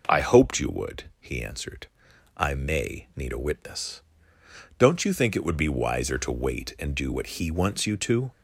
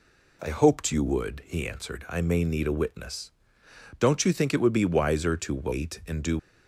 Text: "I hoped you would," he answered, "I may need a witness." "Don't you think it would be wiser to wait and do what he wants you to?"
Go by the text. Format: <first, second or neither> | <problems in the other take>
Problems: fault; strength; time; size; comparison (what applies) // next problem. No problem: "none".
first | stops before "what he wants you to"; at 6.3 s